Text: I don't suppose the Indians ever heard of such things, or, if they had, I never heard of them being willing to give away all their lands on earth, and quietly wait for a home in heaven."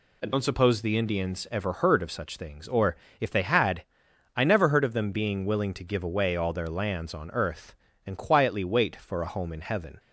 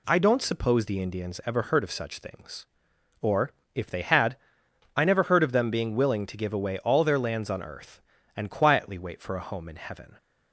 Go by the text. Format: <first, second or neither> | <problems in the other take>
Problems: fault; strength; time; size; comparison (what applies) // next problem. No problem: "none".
neither | none